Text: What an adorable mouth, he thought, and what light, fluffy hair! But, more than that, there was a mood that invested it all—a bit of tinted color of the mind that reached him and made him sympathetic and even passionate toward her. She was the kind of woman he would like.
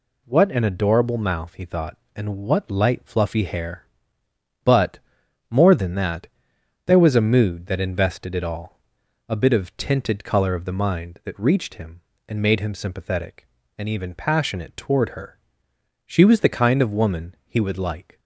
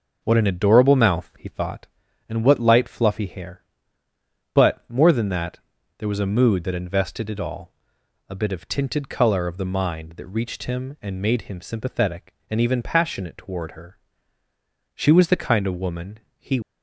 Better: first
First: none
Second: pauses between "woman" and "he"; slight; at 16.1 s; 0.18 s long // stops before "would like"; at 16.6 s

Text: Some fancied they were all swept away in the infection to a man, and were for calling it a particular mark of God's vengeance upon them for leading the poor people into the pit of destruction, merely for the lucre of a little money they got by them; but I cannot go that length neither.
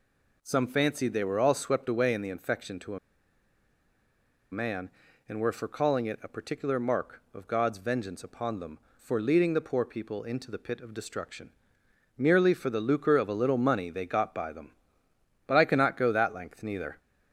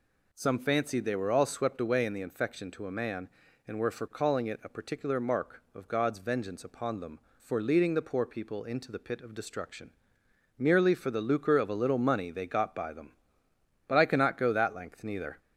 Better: second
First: pauses between "a" and "man"; strong; at 2.9 s; 1.5 s long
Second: none

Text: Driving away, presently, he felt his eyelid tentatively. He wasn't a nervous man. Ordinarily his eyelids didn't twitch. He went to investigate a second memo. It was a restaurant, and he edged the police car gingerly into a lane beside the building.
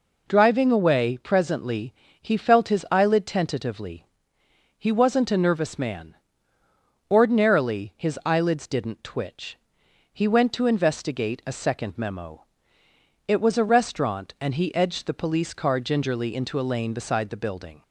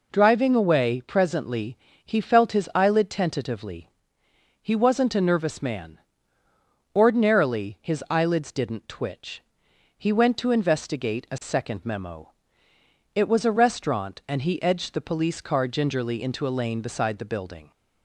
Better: neither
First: none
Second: none

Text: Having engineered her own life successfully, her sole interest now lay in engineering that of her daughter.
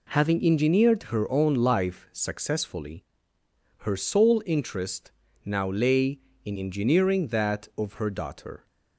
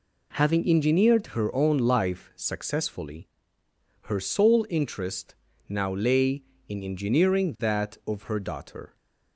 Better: neither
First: pauses between "interest" and "now"; slight; at 5.1 s; 0.32 s long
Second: pauses between "interest" and "now"; slight; at 5.3 s; 0.32 s long

